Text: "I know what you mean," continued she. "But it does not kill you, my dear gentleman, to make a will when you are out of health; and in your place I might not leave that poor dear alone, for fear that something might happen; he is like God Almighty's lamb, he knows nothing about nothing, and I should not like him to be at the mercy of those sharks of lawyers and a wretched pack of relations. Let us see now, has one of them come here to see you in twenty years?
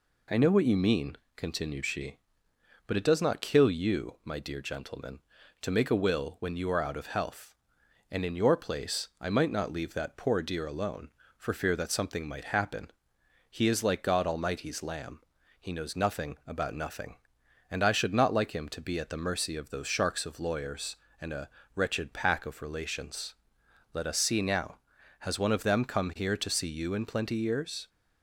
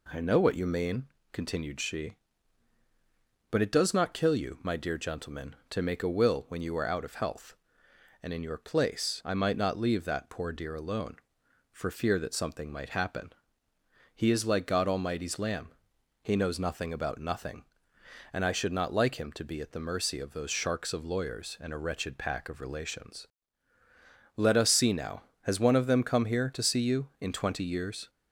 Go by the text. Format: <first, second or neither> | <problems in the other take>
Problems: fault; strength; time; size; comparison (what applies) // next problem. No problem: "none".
second | pauses between "a" and "wretched"; slight; at 21.4 s; 0.24 s long // says "plenty" for "twenty"; at 27.0 s